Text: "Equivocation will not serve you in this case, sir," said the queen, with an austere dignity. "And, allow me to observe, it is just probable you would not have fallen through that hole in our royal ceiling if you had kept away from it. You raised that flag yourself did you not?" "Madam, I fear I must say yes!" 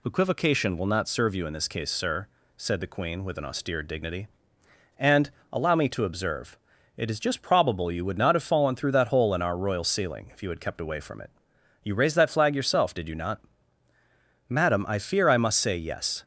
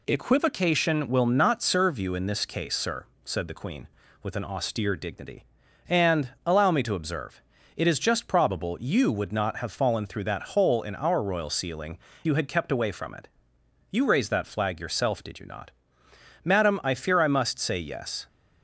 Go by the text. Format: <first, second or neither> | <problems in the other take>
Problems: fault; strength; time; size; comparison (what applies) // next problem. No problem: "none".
first | skips "if"; at 12.1 s